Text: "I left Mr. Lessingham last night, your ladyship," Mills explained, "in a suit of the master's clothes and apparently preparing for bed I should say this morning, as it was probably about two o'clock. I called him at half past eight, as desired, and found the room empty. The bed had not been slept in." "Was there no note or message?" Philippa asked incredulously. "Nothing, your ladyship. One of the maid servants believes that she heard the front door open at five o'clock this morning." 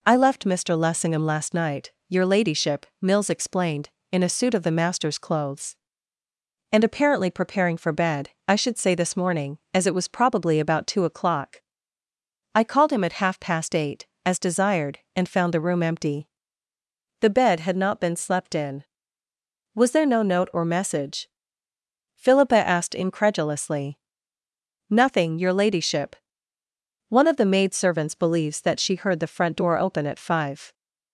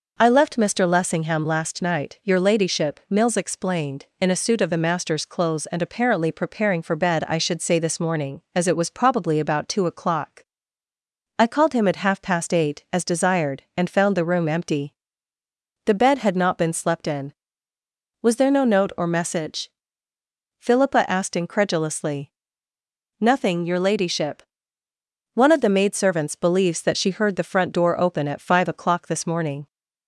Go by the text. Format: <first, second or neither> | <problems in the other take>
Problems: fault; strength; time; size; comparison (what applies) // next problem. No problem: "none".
second | pauses between "bed" and "I"; slight; at 8.2 s; 0.18 s long // stops before "o'clock this morning"; at 30.7 s